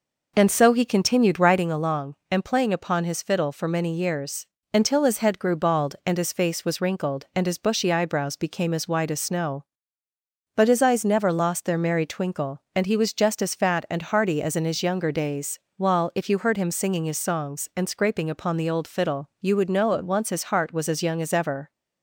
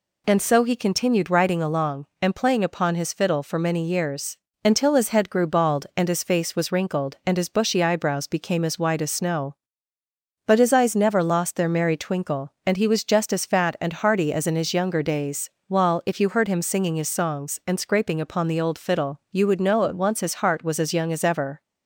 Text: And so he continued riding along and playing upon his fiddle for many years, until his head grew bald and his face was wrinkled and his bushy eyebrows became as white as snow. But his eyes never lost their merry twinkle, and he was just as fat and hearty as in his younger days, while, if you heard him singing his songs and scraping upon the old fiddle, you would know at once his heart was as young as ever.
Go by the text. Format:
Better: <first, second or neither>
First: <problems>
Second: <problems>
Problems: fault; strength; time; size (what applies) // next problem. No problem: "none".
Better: second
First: starts louder than the rest; noticeable; until 1.6 s; 5 dB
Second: none